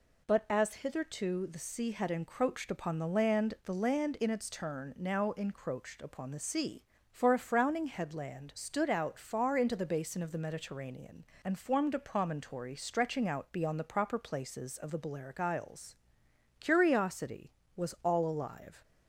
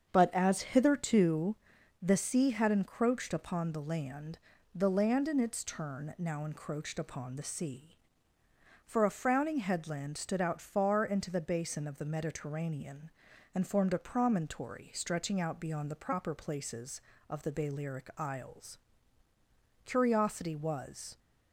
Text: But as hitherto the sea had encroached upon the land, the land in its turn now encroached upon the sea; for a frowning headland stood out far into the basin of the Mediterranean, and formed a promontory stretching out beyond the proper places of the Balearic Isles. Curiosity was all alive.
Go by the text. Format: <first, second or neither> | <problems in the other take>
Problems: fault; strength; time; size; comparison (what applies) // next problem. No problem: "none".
first | starts louder than the rest; until 1.1 s; 7 dB // pauses between "hitherto" and "the"; noticeable; at 1.5 s; 0.46 s long // stops before "all alive"; at 21.1 s